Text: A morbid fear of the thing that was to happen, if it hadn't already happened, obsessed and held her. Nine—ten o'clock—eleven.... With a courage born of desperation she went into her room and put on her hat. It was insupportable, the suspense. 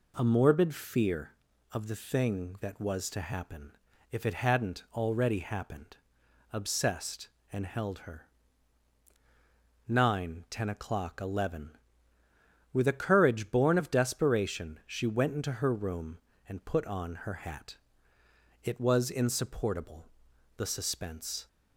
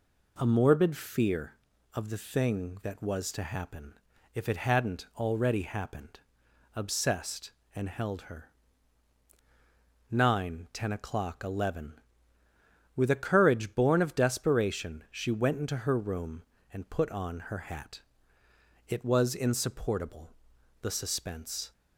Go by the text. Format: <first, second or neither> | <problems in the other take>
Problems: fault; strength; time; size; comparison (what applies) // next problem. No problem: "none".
neither | none